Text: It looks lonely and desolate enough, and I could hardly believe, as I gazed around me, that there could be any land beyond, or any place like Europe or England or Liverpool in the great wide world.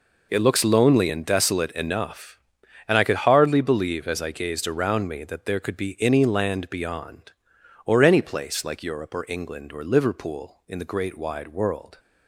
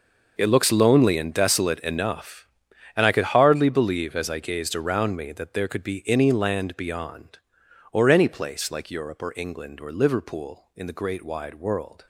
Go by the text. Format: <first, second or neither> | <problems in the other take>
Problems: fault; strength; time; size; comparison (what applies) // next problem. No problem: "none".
first | gets quieter; strong; throughout; 15 dB